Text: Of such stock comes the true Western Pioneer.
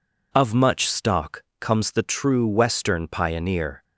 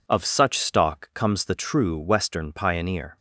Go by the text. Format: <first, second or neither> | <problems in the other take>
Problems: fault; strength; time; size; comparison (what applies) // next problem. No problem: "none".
second | says "much" for "such"; at 0.5 s // pauses between "stock" and "comes"; slight; at 1.4 s; 0.16 s long